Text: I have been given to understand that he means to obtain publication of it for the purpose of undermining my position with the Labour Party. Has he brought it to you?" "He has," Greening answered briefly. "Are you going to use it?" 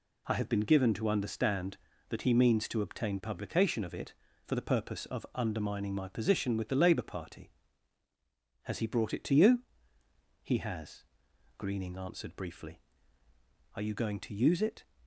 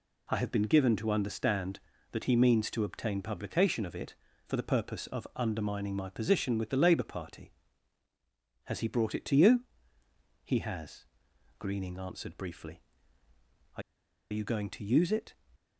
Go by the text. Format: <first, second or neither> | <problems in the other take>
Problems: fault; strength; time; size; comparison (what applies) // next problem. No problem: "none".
first | pauses between "Are" and "you"; noticeable; at 13.8 s; 0.49 s long